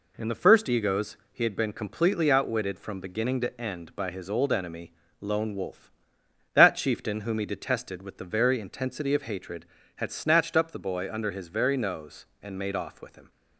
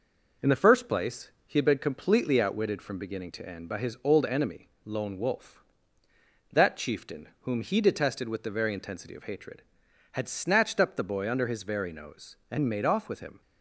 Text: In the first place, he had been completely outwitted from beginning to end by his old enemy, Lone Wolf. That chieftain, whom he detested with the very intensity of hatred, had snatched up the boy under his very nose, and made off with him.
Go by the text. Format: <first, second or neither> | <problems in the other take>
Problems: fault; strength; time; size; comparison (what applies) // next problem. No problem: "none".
second | says "egos" for "place"; at 0.6 s